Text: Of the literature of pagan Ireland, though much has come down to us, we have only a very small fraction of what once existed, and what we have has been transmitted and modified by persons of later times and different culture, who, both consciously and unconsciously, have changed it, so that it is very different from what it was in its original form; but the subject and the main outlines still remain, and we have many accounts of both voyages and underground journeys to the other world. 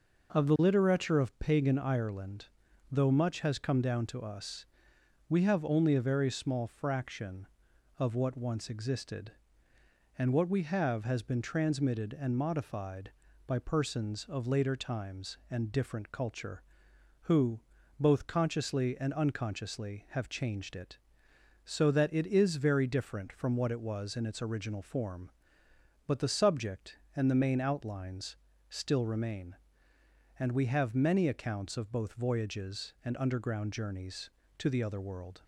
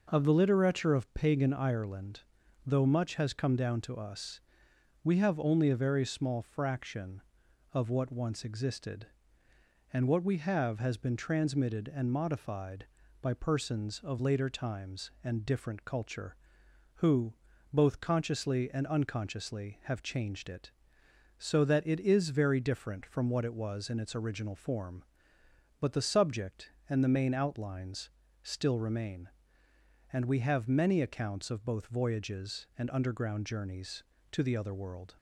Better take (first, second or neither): neither